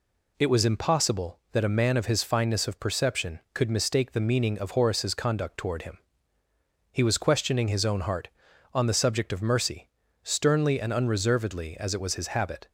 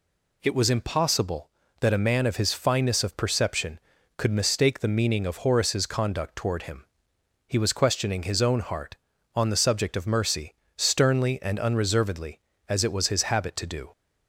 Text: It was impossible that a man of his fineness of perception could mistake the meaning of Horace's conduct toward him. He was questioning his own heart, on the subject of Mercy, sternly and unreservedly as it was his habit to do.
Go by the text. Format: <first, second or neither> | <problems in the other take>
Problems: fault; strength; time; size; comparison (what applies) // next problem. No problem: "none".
second | stops before "to do"; at 12.6 s